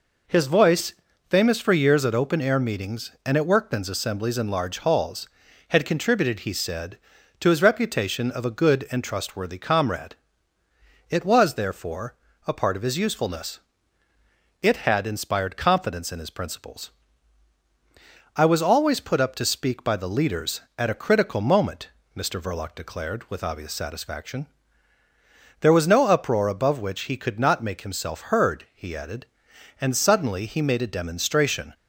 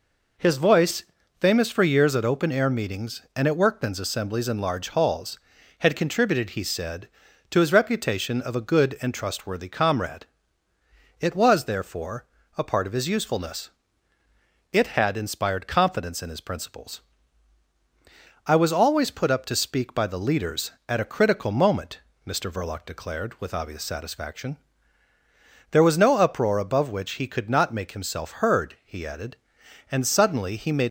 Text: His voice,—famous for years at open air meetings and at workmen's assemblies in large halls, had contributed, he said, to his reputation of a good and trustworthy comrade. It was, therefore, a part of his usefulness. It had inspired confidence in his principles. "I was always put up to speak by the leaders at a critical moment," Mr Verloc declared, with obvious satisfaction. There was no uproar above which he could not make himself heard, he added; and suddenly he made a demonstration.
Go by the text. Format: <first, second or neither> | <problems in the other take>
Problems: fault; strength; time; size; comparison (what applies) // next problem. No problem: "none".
first | stops before "a demonstration"; at 30.8 s